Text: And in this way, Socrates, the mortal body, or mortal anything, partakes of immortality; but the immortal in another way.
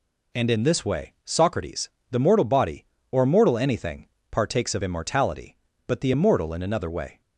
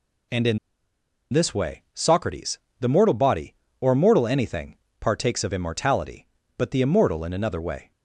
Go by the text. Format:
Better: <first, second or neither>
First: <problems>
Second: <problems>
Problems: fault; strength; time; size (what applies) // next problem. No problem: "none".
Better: first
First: none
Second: pauses between "in" and "this"; noticeable; at 0.5 s; 0.75 s long